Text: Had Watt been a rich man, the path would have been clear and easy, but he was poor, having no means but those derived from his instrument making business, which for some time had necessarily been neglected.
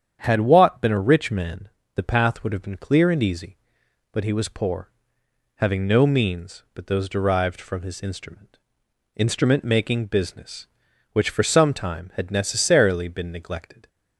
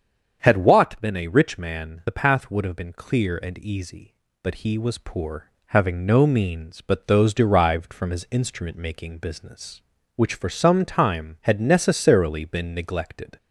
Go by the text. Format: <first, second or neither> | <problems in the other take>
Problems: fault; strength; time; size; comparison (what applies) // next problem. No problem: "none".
second | starts louder than the rest; strong; until 1.2 s; 8.5 dB; strong in the second // says "instrument" twice; at 9.1 s